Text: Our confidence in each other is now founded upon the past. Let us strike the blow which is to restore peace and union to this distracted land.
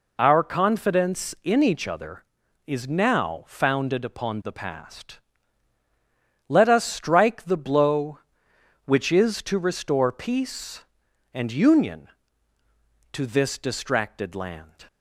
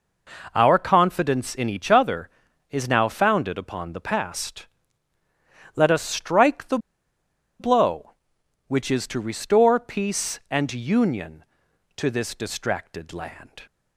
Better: first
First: none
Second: pauses between "the" and "blow"; noticeable; at 6.7 s; 0.81 s long

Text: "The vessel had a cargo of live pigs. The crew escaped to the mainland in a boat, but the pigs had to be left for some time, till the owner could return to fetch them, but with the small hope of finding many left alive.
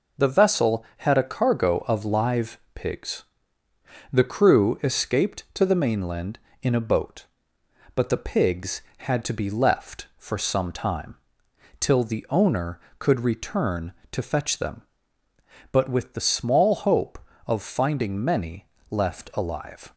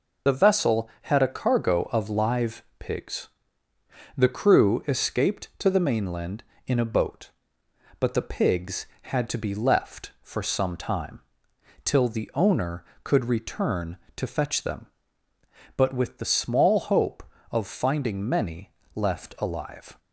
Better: first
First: pauses between "live" and "pigs"; slight; at 2.5 s; 0.16 s long // pauses between "many" and "left"; slight; at 18.6 s; 0.24 s long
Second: loses the start of "The"; at 0.2 s; 35 ms // pauses between "live" and "pigs"; slight; at 2.6 s; 0.16 s long // pauses between "many" and "left"; slight; at 18.7 s; 0.24 s long

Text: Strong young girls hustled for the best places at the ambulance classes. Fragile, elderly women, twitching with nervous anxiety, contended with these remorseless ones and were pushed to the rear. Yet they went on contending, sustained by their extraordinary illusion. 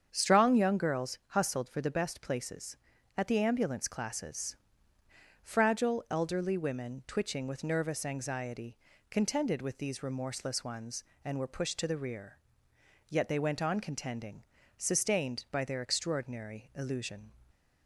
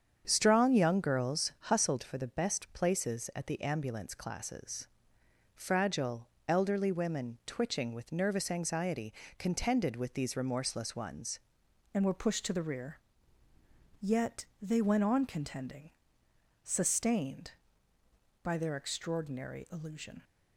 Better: first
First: starts louder than the rest; strong; until 1.1 s; 7.5 dB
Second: starts louder than the rest; strong; until 1.2 s; 7.5 dB // changes voice at "and"; from 11.9 s on; 8.3 s long // pauses between "Yet" and "they"; slight; at 14.4 s; 0.18 s long

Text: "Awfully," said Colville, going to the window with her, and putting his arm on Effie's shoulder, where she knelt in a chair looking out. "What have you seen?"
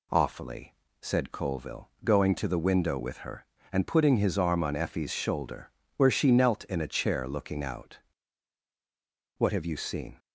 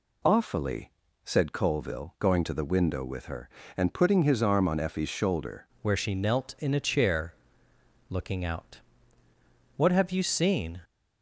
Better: first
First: none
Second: changes voice at "where"; from 5.8 s on; 4.9 s long // pauses between "chair" and "looking"; noticeable; at 7.3 s; 0.76 s long

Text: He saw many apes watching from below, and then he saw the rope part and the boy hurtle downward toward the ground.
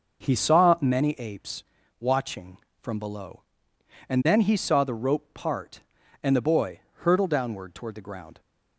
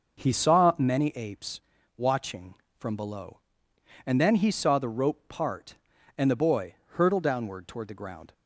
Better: neither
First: pauses between "apes" and "watching"; slight; at 1.6 s; 0.36 s long // pauses between "boy" and "hurtle"; slight; at 6.7 s; 0.20 s long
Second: pauses between "apes" and "watching"; slight; at 1.6 s; 0.36 s long // pauses between "boy" and "hurtle"; slight; at 6.7 s; 0.18 s long

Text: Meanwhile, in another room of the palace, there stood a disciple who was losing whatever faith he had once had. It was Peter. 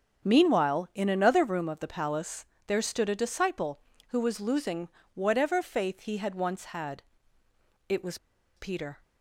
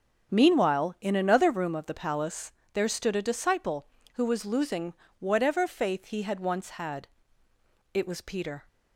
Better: second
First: starts louder than the rest; strong; until 1.3 s; 7.5 dB // pauses between "losing" and "whatever"; slight; at 4.8 s; 0.26 s long // pauses between "was" and "Peter"; at 8.1 s; 0.40 s long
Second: starts louder than the rest; strong; until 1.3 s; 7.5 dB // pauses between "losing" and "whatever"; slight; at 4.9 s; 0.26 s long

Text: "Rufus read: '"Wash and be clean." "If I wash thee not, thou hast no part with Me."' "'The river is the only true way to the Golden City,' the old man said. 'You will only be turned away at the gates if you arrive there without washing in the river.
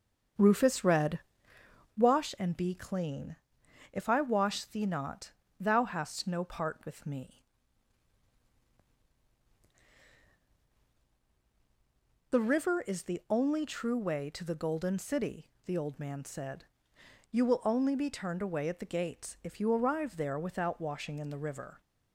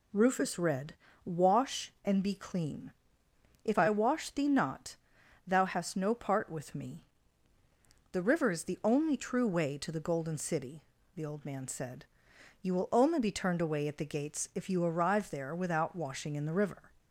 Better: second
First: starts louder than the rest; until 2.0 s; 7 dB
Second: none

